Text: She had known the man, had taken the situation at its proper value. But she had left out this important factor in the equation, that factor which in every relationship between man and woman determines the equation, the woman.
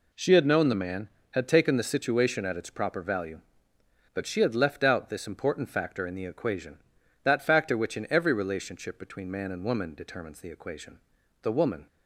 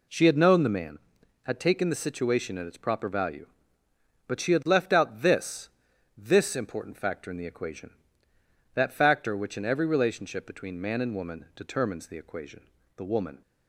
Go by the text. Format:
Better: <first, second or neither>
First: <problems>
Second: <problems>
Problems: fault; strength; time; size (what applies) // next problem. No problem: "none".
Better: first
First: none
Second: says "this" twice; at 6.1 s